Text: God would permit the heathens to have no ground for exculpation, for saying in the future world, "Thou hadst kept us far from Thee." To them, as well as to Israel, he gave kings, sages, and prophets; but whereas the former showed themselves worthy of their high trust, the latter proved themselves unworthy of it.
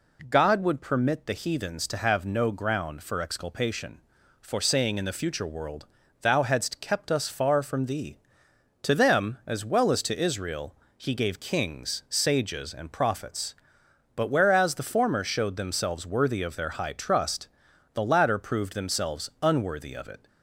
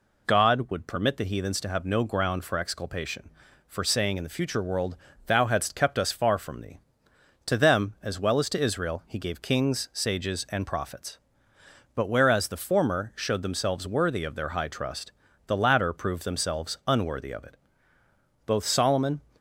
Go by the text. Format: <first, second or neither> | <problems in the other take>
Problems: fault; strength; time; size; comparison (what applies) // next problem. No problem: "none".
first | goes on to say "Both Solomon"; noticeable; from 18.4 s on; 0.74 s long